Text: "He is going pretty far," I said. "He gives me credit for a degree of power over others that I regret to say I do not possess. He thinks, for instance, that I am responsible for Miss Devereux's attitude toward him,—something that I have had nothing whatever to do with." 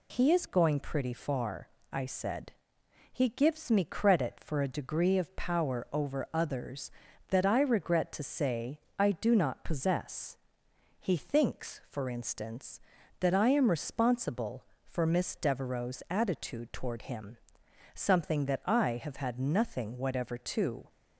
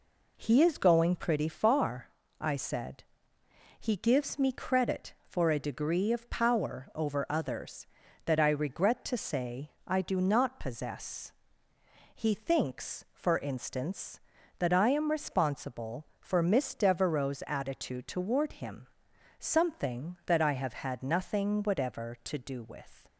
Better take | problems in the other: second | pauses between "say" and "I"; slight; at 8.8 s; 0.18 s long; slight in the second // stops before "do with"; at 20.8 s

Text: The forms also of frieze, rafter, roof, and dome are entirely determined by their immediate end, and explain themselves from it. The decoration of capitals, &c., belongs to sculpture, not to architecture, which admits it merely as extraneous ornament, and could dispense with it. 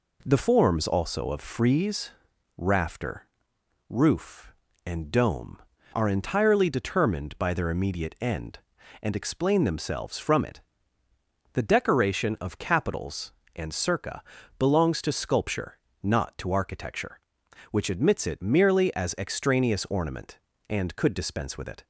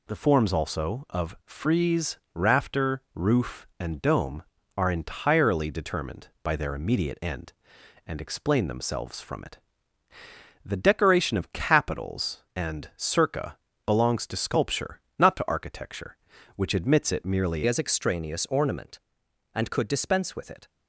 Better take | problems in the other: first | changes voice at "as"; from 17.6 s on; 3.0 s long

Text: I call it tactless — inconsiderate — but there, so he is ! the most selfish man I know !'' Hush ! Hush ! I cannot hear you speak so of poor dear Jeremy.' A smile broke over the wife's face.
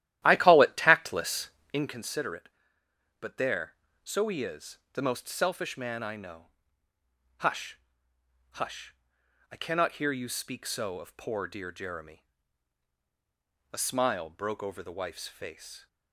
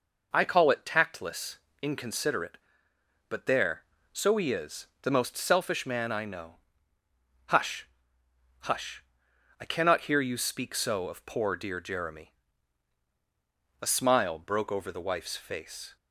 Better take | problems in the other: second | starts louder than the rest; strong; until 2.0 s; 13 dB

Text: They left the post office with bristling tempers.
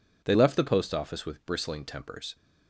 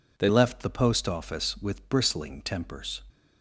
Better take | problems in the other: first | changes voice at "left"; from 0.2 s on; 2.8 s long

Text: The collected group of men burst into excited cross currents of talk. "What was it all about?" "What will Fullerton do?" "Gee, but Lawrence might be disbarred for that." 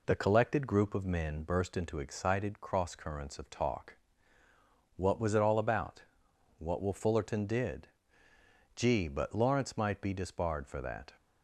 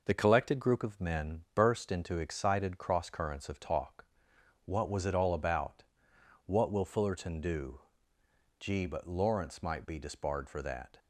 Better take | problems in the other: second | says "did" for "do"; at 7.4 s

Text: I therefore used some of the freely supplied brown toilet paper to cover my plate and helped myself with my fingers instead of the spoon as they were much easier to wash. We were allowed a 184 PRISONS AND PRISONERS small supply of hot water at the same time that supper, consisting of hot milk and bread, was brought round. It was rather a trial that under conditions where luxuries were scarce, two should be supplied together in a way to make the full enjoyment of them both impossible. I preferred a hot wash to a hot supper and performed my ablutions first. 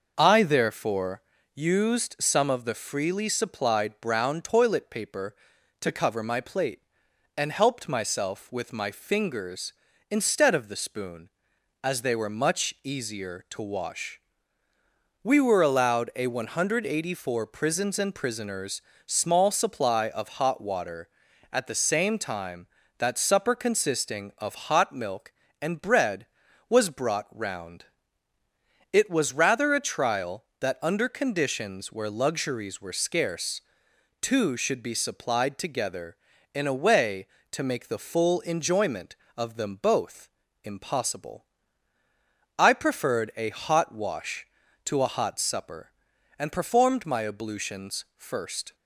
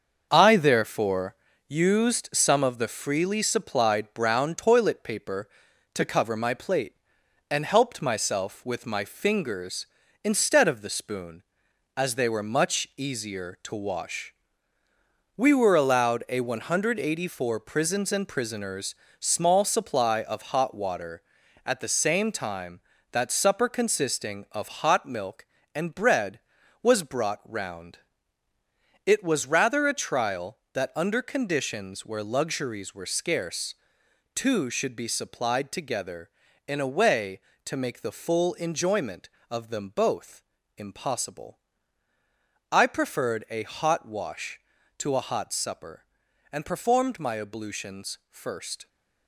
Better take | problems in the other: first | gets quieter; throughout; 6.5 dB // pauses between "therefore" and "used"; slight; at 1.3 s; 0.32 s long; slight in the first // pauses between "PRISONERS" and "small"; slight; at 18.9 s; 0.26 s long; slight in the first // pauses between "both" and "impossible"; slight; at 40.4 s; 0.34 s long; slight in the first

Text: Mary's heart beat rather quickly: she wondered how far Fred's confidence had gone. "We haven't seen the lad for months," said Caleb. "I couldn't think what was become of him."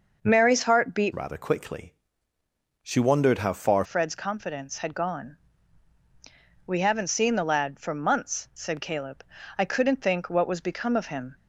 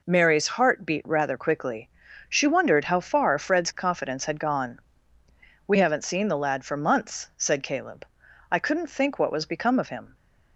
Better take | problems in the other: second | changes voice from "rather" to "far"; from 1.1 to 3.8 s; 2.7 s long

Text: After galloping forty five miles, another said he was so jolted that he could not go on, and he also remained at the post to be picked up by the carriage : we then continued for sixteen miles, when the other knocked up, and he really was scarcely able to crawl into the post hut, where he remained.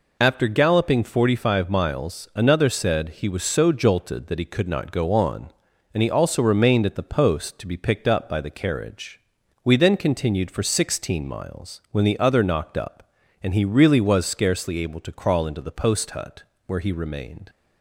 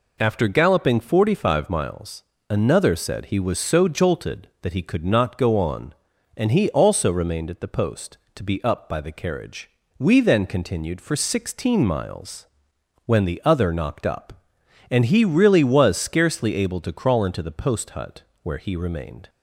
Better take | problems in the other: first | skips "picked"; at 8.6 s

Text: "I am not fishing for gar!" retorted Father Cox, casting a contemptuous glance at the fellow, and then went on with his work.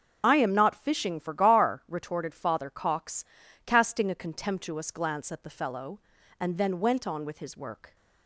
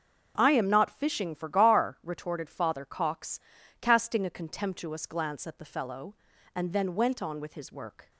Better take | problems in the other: second | loses the start of "I"; at 0.2 s; 40 ms // starts louder than the rest; until 1.2 s; 6 dB; also in the second

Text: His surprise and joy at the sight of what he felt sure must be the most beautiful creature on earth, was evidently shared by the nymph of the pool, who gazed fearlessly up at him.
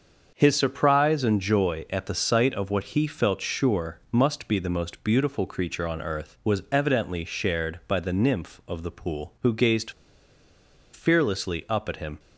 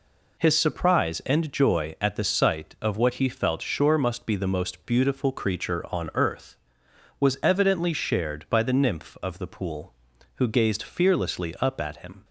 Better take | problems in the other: second | starts louder than the rest; until 1.3 s; 6.5 dB // pauses between "gazed" and "fearlessly"; at 9.9 s; 1.0 s long

